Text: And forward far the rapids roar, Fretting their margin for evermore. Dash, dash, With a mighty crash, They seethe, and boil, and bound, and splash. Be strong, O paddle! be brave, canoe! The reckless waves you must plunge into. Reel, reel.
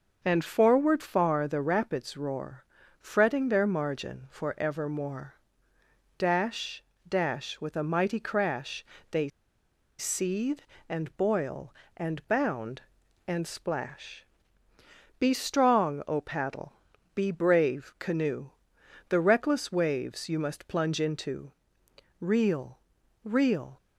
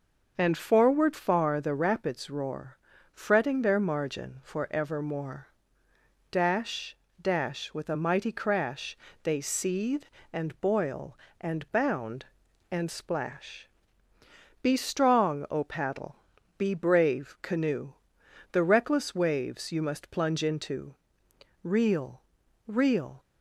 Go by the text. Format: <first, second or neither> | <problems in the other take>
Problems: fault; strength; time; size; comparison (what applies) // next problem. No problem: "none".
second | starts louder than the rest; until 1.2 s; 6 dB; noticeable in the second // pauses between "They" and "seethe"; noticeable; at 9.2 s; 0.70 s long